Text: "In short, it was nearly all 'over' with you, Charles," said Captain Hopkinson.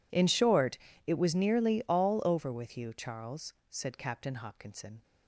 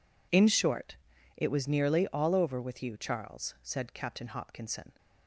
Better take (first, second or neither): neither